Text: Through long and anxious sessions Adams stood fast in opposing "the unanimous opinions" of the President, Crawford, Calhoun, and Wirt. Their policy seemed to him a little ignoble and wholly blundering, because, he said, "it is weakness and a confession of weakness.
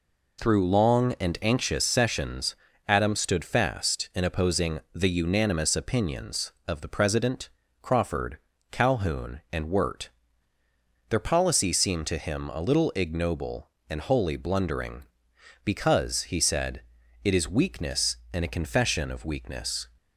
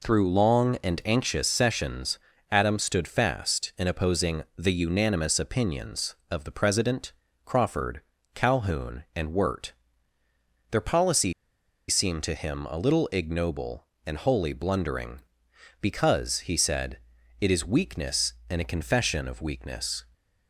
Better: first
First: pauses between "sessions" and "Adams"; slight; at 2.5 s; 0.32 s long // pauses between "opposing" and "the"; slight; at 4.7 s; 0.16 s long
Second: pauses between "sessions" and "Adams"; slight; at 2.1 s; 0.32 s long // pauses between "opposing" and "the"; slight; at 4.4 s; 0.16 s long // pauses between "policy" and "seemed"; noticeable; at 11.3 s; 0.55 s long

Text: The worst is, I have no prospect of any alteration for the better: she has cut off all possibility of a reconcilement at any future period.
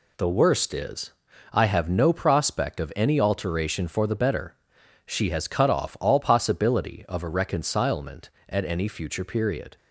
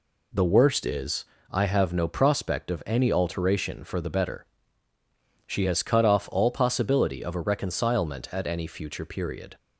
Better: neither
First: none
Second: none

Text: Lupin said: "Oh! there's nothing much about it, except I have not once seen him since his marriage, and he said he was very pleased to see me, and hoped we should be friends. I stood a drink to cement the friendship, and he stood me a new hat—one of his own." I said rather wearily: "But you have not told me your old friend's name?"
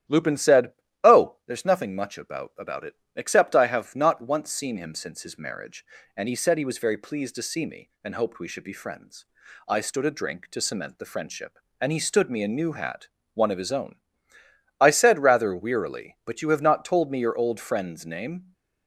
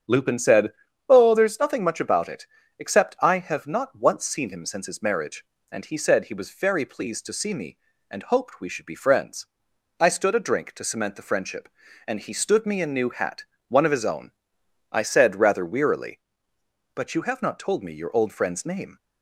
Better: second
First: starts louder than the rest; strong; until 1.5 s; 11.5 dB // says "about" twice; at 2.5 s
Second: starts louder than the rest; strong; until 1.4 s; 8.5 dB

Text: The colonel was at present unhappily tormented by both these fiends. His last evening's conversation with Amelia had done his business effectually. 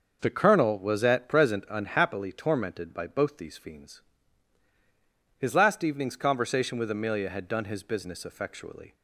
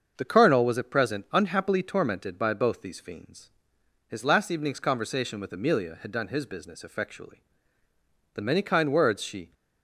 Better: first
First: starts louder than the rest; until 1.2 s; 6.5 dB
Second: starts louder than the rest; until 1.1 s; 6.5 dB // goes on to say "The many kind words she"; noticeable; from 8.3 s on; 1.1 s long

